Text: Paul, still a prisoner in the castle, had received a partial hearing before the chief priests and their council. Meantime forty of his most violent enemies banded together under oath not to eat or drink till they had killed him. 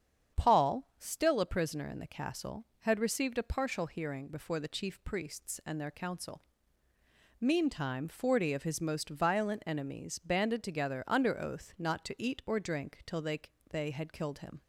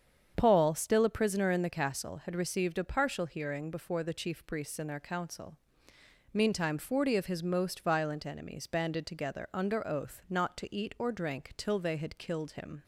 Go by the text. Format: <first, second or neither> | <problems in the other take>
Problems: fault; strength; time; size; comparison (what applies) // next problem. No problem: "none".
second | starts louder than the rest; strong; until 1.4 s; 8 dB; strong in the second // says "they" twice; at 13.6 s